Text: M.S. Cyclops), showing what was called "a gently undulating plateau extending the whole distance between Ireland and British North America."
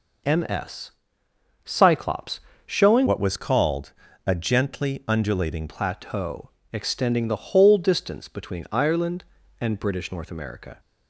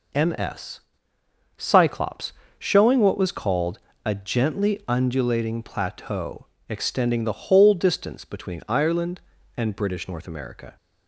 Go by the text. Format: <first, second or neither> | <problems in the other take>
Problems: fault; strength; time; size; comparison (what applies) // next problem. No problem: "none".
second | changes voice from "what" to "undulating"; from 3.0 to 5.6 s; 2.6 s long // pauses between "called" and "a"; slight; at 3.9 s; 0.34 s long; slight in the second // pauses between "plateau" and "extending"; slight; at 6.4 s; 0.24 s long; slight in the second